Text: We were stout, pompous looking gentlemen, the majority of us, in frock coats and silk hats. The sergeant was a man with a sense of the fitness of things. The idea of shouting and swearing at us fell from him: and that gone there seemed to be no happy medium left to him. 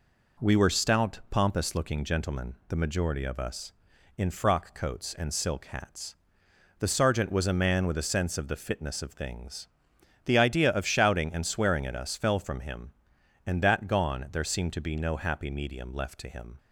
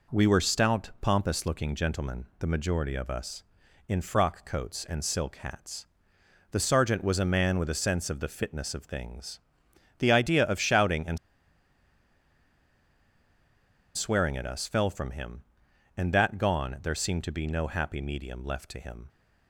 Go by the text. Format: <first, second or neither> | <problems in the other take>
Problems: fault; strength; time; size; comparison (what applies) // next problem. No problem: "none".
first | pauses between "and" and "swearing"; strong; at 11.1 s; 2.7 s long